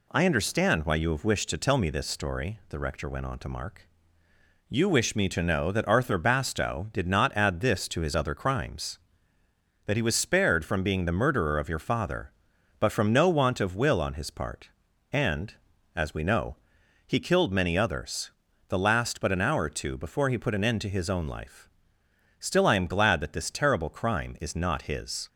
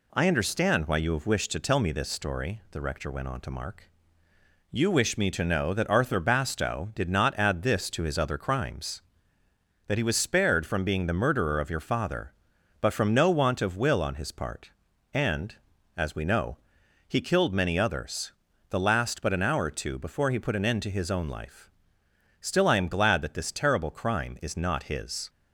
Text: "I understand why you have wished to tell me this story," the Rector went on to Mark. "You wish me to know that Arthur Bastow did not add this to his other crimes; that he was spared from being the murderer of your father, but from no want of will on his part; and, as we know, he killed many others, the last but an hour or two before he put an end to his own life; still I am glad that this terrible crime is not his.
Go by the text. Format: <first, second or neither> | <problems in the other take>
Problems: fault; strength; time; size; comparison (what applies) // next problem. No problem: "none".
neither | none